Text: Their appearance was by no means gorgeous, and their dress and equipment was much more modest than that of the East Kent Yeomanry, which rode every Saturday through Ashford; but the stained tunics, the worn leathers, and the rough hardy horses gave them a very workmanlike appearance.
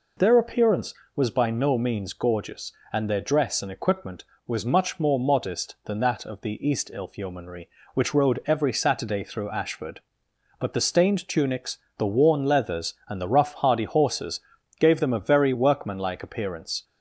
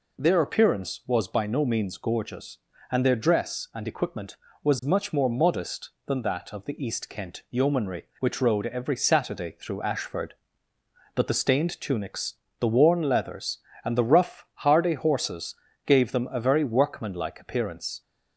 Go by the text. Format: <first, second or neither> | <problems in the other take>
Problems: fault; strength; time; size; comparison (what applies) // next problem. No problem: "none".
second | says "Ilf" for "Kent"; at 6.9 s // pauses between "horses" and "gave"; at 14.4 s; 0.40 s long; slight in the second